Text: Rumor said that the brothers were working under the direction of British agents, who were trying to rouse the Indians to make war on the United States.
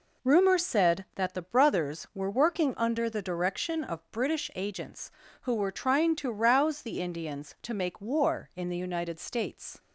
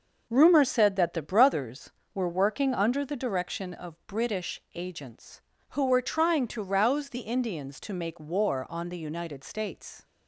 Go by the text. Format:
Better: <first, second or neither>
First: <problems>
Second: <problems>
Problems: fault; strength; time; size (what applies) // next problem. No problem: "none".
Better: second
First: says "in" for "on"; at 8.5 s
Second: none